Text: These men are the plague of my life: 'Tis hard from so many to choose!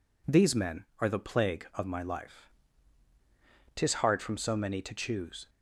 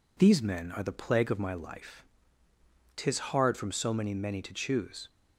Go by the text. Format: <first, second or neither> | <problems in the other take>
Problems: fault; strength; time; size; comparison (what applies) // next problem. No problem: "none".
first | says "many" twice; at 4.1 s